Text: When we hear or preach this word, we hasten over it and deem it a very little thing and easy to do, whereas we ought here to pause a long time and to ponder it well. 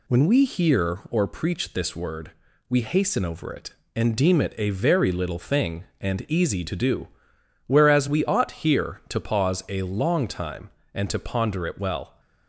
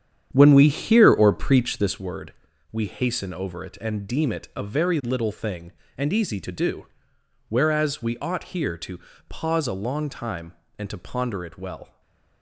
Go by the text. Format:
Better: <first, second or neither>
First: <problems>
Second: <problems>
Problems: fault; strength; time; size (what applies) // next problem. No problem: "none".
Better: first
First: none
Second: starts louder than the rest; strong; until 2.1 s; 9 dB // pauses between "to" and "pause"; slight; at 8.9 s; 0.30 s long // stays silent after the last word; slight; from 11.8 s on; 0.6 s long